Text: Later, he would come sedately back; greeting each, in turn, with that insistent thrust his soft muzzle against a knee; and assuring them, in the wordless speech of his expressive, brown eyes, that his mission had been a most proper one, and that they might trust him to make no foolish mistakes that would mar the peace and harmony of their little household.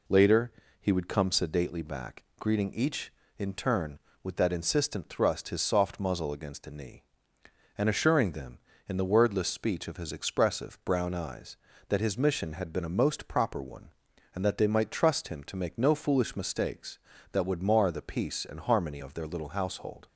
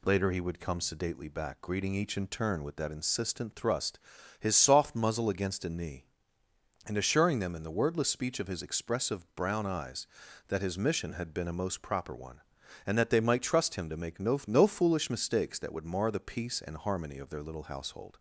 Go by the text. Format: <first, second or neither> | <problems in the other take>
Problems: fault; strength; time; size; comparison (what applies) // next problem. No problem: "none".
first | pauses between "thrust" and "his"; at 3.9 s; 0.40 s long // says "no" twice; at 14.4 s